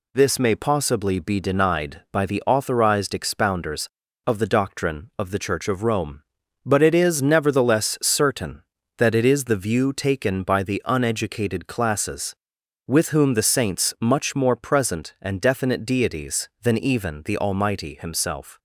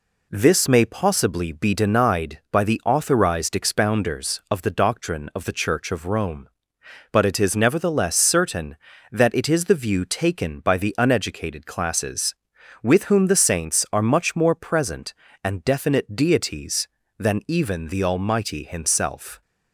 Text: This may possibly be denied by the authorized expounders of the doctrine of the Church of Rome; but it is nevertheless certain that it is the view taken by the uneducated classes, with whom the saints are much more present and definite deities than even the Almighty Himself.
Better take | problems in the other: second | skips "are"; at 13.9 s

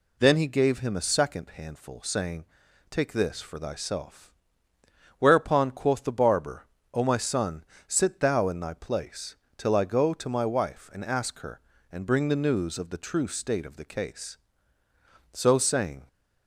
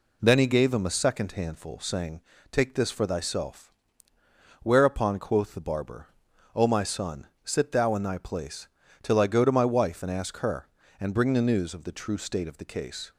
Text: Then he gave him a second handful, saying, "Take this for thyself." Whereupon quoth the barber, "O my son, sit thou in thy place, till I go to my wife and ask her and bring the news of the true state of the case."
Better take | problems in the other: second | goes on to say "So saying"; noticeable; from 15.3 s on; 0.74 s long

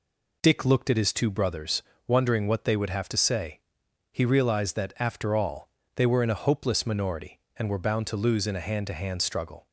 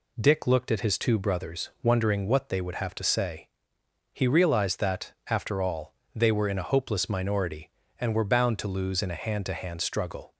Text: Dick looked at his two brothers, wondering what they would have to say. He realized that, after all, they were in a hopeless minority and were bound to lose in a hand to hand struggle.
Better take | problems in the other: neither | none

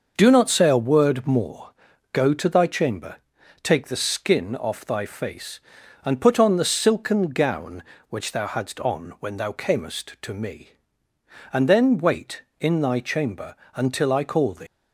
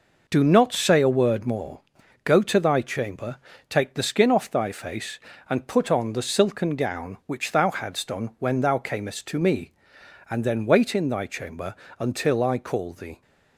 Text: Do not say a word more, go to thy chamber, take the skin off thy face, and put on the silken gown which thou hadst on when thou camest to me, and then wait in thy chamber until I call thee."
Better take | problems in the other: second | pauses between "chamber" and "until"; slight; at 13.5 s; 0.18 s long; slight in the second // leaves "thee" unfinished; at 14.6 s; 115 ms

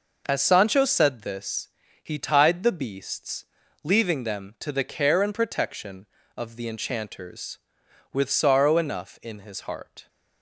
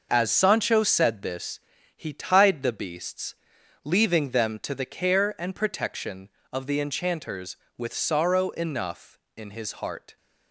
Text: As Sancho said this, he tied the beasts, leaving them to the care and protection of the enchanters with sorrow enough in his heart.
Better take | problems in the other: neither | none

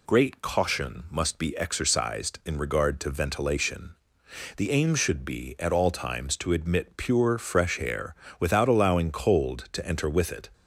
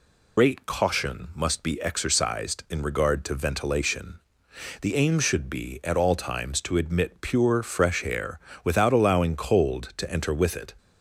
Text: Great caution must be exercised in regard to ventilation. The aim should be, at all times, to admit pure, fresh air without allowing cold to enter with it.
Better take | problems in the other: first | loses the start of "Great"; at 0.3 s; 65 ms // pauses between "air" and "without"; slight; at 8.3 s; 0.24 s long; slight in the first

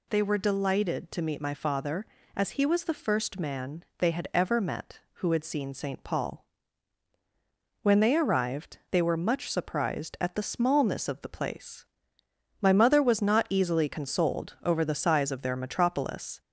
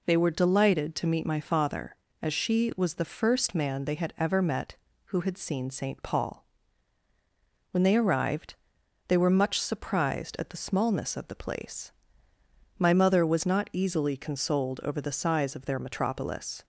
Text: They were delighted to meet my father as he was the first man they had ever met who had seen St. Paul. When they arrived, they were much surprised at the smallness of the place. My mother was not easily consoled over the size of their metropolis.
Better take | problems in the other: first | says "she" for "he"; at 2.3 s

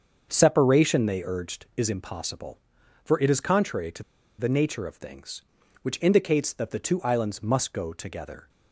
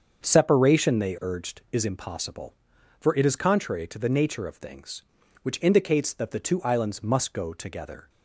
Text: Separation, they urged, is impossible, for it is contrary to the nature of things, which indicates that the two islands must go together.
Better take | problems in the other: second | starts louder than the rest; until 1.3 s; 7 dB; also in the second // pauses between "to" and "the"; slight; at 4.0 s; 0.35 s long

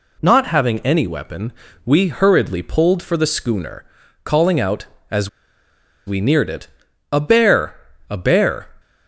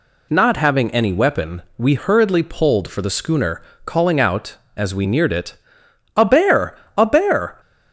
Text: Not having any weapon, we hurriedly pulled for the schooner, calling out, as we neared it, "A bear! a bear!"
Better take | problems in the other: second | pauses between "as" and "we"; noticeable; at 5.2 s; 0.77 s long

